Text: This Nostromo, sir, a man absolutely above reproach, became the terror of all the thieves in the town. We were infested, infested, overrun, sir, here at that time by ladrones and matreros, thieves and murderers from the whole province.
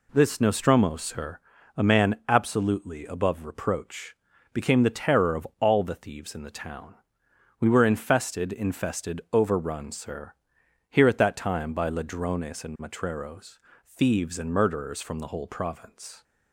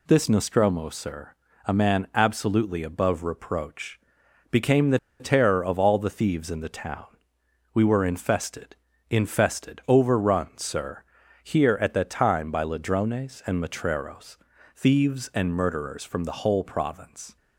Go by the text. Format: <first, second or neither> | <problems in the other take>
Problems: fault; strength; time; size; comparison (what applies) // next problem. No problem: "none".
first | pauses between "the" and "terror"; slight; at 4.9 s; 0.22 s long